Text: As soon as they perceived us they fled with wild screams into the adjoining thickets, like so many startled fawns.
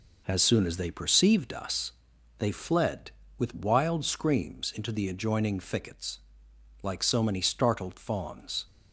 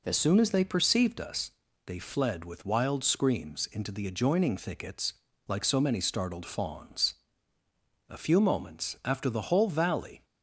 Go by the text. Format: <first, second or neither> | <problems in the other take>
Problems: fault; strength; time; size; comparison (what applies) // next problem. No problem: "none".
first | pauses between "us" and "they"; slight; at 1.5 s; 0.36 s long; noticeable in the first // goes on to say "A few moments after the whole valley"; strong; from 8.0 s on; 2.1 s long